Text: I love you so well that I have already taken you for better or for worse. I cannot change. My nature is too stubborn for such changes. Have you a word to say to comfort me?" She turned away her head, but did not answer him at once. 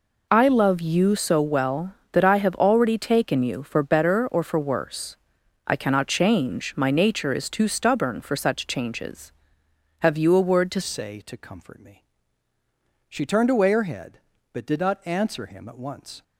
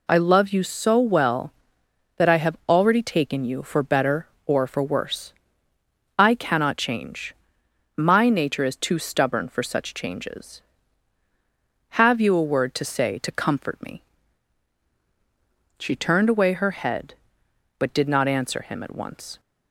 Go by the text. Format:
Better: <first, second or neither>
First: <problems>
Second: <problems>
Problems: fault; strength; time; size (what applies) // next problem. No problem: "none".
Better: second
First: changes voice at "say"; from 10.8 s on; 5.4 s long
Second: none